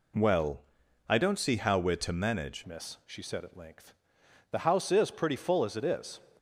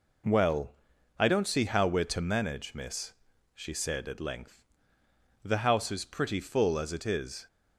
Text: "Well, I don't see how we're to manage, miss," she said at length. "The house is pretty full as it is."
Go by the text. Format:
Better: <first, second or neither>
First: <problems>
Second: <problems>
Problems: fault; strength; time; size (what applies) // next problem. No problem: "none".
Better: second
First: changes voice at "miss"; from 2.6 s on; 3.5 s long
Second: none